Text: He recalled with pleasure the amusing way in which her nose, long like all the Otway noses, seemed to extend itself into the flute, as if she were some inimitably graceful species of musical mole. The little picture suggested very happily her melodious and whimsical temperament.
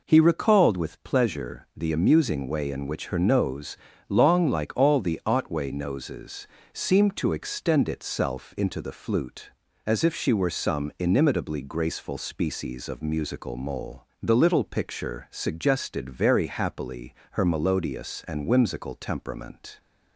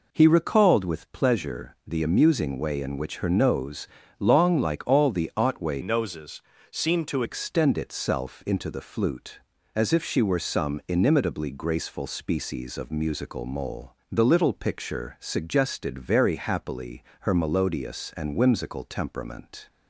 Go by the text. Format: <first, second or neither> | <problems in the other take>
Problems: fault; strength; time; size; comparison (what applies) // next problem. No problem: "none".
first | changes voice from "noses" to "to"; from 5.8 to 7.2 s; 1.4 s long // pauses between "happily" and "her"; slight; at 17.0 s; 0.18 s long; slight in the first